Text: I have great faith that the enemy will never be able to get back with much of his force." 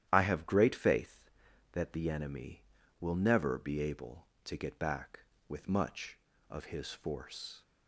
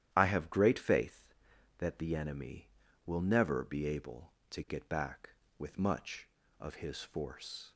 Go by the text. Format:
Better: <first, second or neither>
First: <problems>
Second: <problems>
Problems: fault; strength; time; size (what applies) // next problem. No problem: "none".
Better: neither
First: starts louder than the rest; strong; until 1.1 s; 11.5 dB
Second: starts louder than the rest; strong; until 1.1 s; 11.5 dB